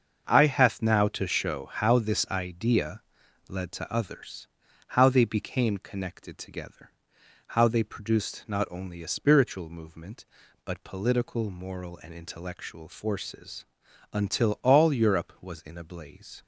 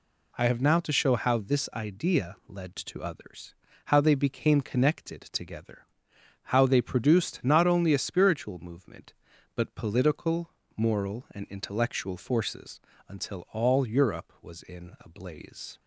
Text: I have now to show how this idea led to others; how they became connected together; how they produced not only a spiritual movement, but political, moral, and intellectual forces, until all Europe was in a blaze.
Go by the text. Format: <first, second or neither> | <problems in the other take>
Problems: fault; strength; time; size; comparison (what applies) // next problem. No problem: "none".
second | starts louder than the rest; until 1.3 s; 6.5 dB // says "hath" for "have"; at 0.4 s // pauses between "idea" and "led"; noticeable; at 3.0 s; 0.46 s long